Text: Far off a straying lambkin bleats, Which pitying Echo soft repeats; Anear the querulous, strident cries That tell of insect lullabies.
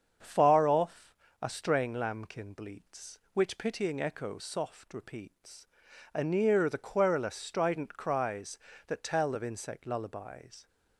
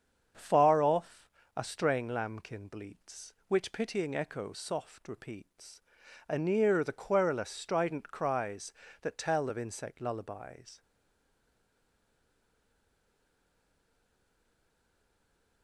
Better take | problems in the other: first | starts louder than the rest; strong; until 1.6 s; 7 dB; strong in the first // pauses between "off" and "a"; slight; at 1.2 s; 0.28 s long; slight in the first // stays silent after the last word; strong; from 10.8 s on; 4.8 s long

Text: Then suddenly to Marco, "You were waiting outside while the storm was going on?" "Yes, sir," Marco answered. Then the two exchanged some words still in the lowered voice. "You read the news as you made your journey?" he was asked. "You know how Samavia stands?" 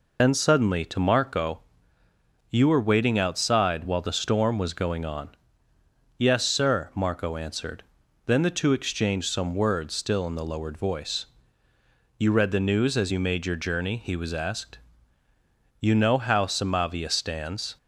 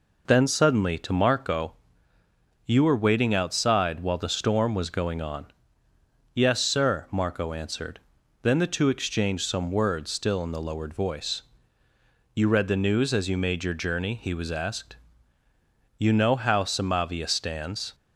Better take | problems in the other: second | loses the start of "Then"; at 0.1 s; 70 ms

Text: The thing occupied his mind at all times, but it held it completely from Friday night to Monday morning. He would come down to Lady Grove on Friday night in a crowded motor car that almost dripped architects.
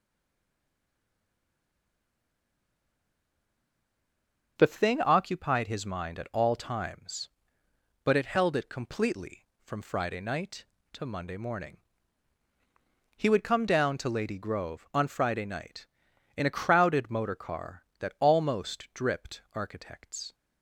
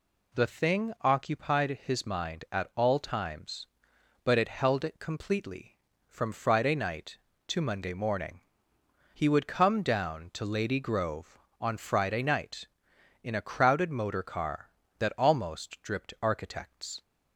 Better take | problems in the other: second | stays silent before the first word; strong; until 4.5 s; 4.5 s long

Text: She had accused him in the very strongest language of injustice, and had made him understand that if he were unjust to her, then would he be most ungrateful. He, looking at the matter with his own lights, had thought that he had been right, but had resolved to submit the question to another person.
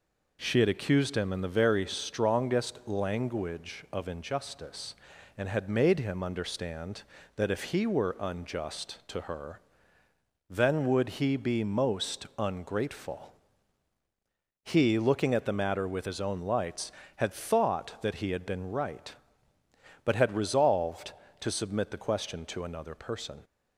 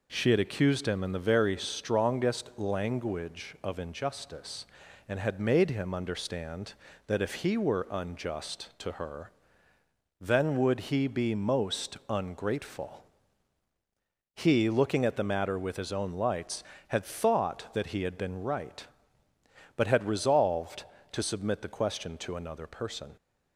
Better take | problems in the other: neither | none

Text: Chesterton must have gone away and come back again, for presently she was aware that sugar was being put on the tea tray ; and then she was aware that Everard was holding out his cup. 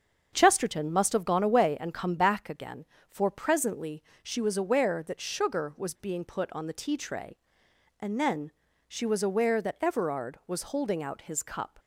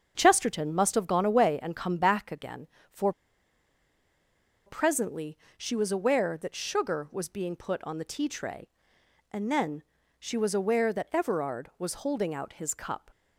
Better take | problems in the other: first | starts louder than the rest; until 1.1 s; 7 dB; also in the first // pauses between "for" and "presently"; strong; at 3.1 s; 1.5 s long // pauses between "presently" and "she"; slight; at 5.3 s; 0.22 s long; slight in the first // pauses between "then" and "she"; slight; at 9.8 s; 0.36 s long; slight in the first

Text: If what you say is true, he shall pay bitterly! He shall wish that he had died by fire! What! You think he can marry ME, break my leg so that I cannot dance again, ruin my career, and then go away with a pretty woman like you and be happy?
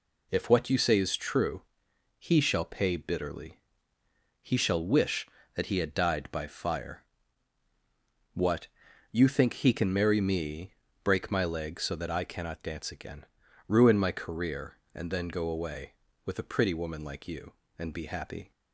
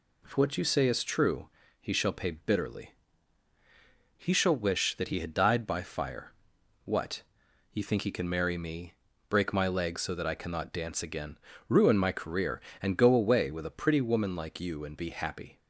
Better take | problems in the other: first | skips "then"; at 12.9 s

